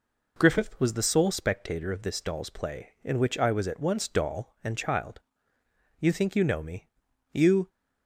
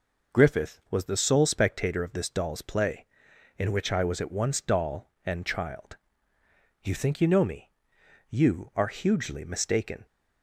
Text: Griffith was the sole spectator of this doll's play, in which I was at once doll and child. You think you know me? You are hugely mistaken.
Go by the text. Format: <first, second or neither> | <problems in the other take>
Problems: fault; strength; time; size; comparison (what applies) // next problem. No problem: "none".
second | stops before "are hugely mistaken"; at 7.6 s